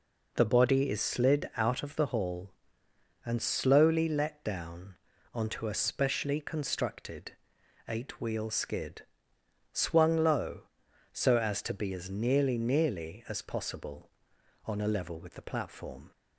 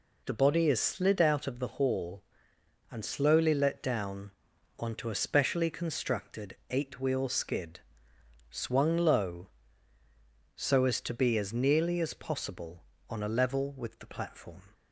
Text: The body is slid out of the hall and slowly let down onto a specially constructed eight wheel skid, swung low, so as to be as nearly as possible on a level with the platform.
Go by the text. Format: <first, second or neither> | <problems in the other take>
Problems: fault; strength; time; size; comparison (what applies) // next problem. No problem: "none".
second | pauses between "down" and "onto"; at 4.9 s; 0.38 s long; noticeable in the second // pauses between "constructed" and "eight"; noticeable; at 7.3 s; 0.56 s long // says "nearly" twice; at 12.5 s